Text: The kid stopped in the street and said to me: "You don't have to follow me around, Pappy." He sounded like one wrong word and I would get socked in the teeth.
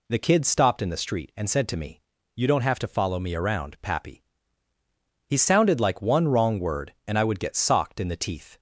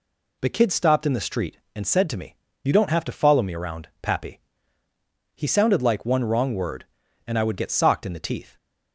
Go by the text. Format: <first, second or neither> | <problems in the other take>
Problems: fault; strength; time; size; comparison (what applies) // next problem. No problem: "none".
neither | none